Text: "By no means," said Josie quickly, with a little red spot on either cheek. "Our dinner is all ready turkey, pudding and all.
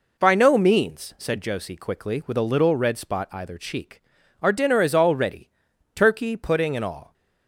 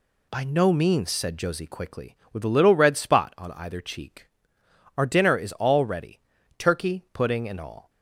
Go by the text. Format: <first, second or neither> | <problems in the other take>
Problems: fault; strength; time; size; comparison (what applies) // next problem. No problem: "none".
second | skips "on"; at 3.2 s // pauses between "ready" and "turkey"; at 5.5 s; 0.42 s long; also in the second